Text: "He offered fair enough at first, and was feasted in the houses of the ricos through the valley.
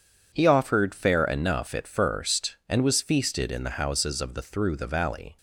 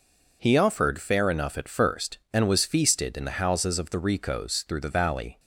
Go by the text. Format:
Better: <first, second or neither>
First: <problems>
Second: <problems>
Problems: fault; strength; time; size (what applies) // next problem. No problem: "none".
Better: second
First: skips "ricos"; at 4.4 s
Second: none